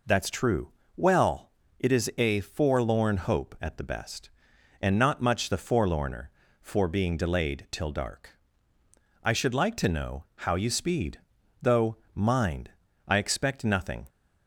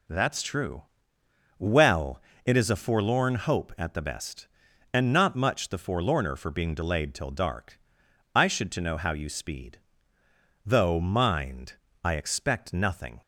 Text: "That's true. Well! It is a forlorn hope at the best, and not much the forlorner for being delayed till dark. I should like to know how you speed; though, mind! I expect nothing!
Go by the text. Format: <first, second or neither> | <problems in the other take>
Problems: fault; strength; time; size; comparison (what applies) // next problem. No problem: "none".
first | skips "like"; at 8.7 s